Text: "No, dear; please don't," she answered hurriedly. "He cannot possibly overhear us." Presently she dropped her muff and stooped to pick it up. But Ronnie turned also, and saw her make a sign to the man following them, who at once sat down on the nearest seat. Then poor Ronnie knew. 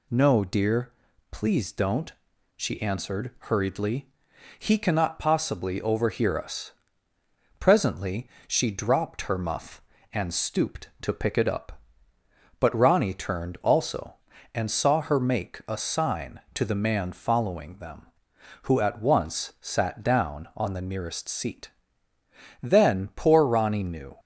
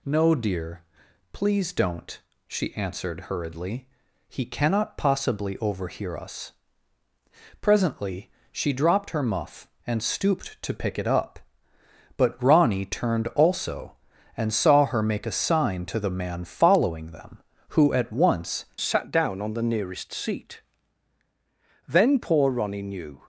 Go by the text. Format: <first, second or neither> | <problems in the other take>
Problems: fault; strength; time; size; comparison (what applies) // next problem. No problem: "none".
first | pauses between "Presently" and "she"; slight; at 8.3 s; 0.20 s long; slight in the first // changes voice at "sat"; from 18.8 s on; 4.4 s long